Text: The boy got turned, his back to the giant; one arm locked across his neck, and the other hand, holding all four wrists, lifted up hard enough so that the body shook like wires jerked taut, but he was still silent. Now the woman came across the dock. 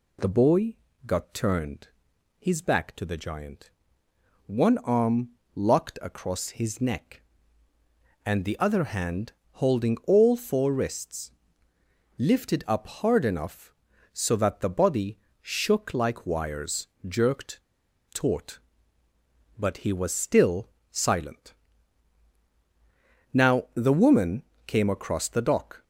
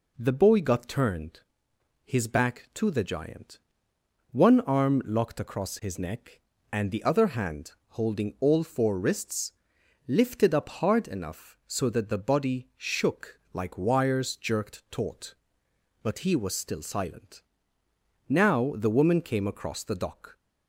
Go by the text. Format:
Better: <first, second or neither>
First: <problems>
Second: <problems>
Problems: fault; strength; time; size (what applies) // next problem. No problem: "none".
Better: second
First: pauses between "boy" and "got"; slight; at 0.7 s; 0.30 s long // pauses between "arm" and "locked"; slight; at 5.2 s; 0.26 s long // pauses between "body" and "shook"; slight; at 15.1 s; 0.24 s long // pauses between "wires" and "jerked"; slight; at 16.8 s; 0.20 s long // pauses between "jerked" and "taut"; noticeable; at 17.6 s; 0.51 s long // pauses between "still" and "silent"; slight; at 20.6 s; 0.24 s long // pauses between "woman" and "came"; slight; at 24.4 s; 0.22 s long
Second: none